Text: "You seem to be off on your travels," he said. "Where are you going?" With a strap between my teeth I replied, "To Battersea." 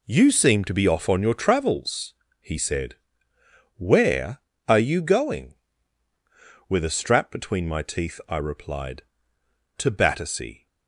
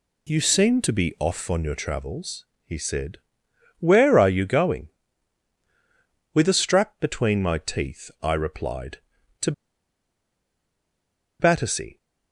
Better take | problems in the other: first | pauses between "To" and "Battersea"; strong; at 9.5 s; 1.8 s long

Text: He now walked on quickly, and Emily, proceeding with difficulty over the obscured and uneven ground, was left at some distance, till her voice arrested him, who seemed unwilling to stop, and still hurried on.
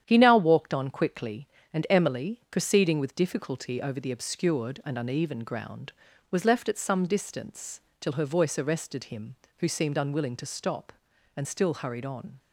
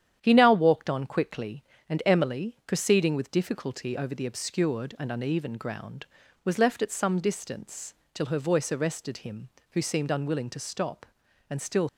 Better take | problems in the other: first | starts louder than the rest; strong; until 1.2 s; 10 dB; strong in the first // stops before "hurried on"; at 11.8 s

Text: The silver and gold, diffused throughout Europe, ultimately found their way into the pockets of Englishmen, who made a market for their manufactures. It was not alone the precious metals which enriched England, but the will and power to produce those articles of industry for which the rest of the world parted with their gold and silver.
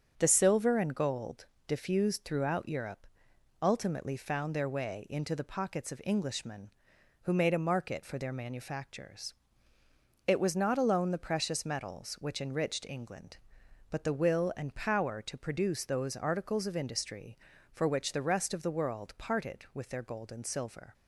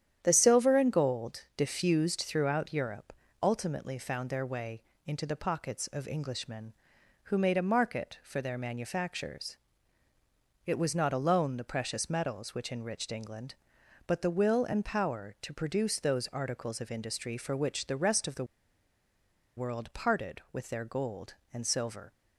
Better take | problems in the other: first | starts louder than the rest; strong; until 1.2 s; 10 dB; also in the first // pauses between "way" and "into"; slight; at 4.8 s; 0.26 s long // pauses between "the" and "world"; at 18.4 s; 1.1 s long

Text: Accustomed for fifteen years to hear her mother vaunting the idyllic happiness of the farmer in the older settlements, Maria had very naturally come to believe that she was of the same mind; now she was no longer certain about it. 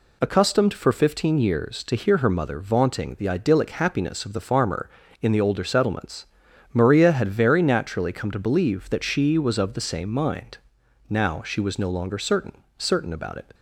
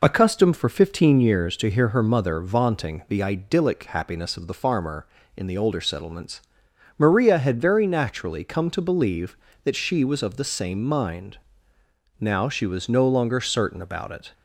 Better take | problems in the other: second | says "certain" twice; at 12.7 s

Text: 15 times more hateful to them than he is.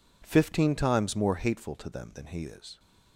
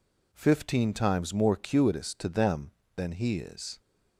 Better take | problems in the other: first | says "cuitous" for "hateful"; at 1.5 s

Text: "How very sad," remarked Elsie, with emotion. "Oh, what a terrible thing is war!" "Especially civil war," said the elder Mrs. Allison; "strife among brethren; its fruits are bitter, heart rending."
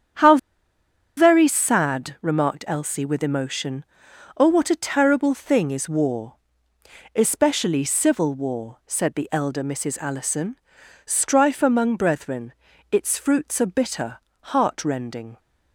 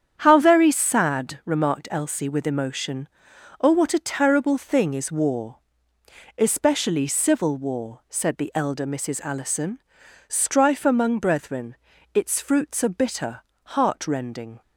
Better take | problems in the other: second | starts louder than the rest; strong; until 2.0 s; 8.5 dB; strong in the second // pauses between "How" and "very"; noticeable; at 0.3 s; 0.80 s long

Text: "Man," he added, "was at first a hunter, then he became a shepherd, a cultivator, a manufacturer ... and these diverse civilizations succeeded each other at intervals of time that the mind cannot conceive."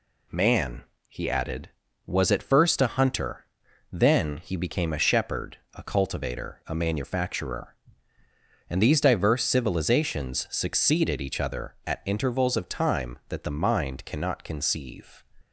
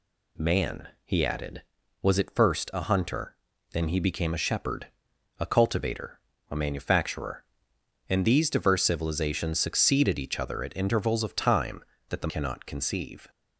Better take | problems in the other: first | skips "mind"; at 12.2 s

